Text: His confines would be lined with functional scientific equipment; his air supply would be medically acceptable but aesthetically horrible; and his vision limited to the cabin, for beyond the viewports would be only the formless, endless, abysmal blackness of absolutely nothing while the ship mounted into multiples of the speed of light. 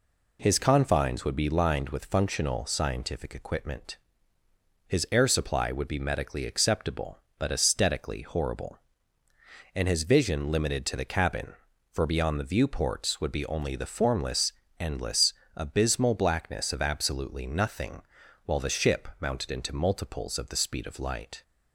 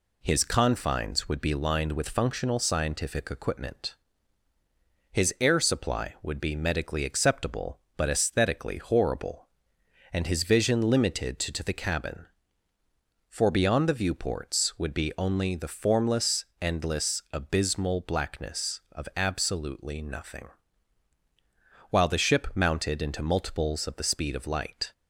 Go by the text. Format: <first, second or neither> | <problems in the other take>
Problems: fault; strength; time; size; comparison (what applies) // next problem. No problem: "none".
first | says "to" twice; at 11.5 s // pauses between "nothing" and "while"; strong; at 20.5 s; 1.4 s long; noticeable in the first